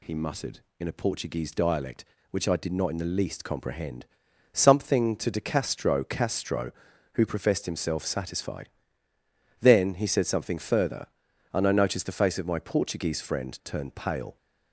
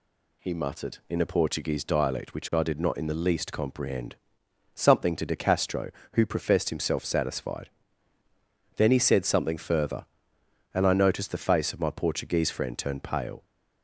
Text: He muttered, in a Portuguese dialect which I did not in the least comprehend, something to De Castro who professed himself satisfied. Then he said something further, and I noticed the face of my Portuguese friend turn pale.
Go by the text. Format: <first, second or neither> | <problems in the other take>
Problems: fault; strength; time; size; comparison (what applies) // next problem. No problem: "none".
second | says "Castro" twice; at 6.0 s